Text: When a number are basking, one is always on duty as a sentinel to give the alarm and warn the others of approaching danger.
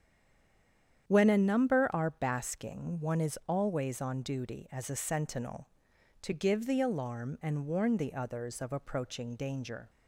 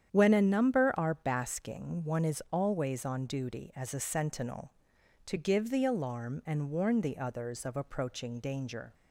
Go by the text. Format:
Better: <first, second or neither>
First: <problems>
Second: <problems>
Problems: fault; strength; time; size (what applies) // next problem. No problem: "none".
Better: second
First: stays silent before the first word; until 1.0 s; 1.0 s long // starts louder than the rest; strong; until 2.1 s; 9 dB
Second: starts louder than the rest; strong; until 1.1 s; 9 dB